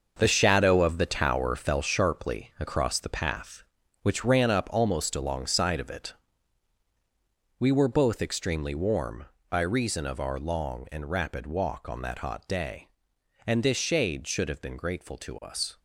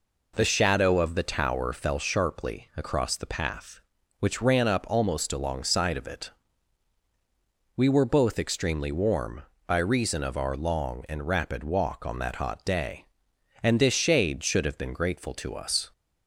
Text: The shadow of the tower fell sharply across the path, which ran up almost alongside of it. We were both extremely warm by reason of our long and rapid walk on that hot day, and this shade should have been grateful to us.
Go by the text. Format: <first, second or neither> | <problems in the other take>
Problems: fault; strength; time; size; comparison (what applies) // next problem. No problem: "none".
second | gets quieter; strong; throughout; 9.5 dB